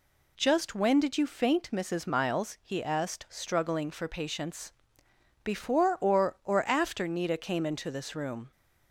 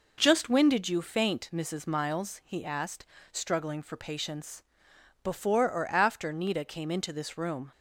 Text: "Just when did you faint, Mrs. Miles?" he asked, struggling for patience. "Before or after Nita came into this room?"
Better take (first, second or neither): second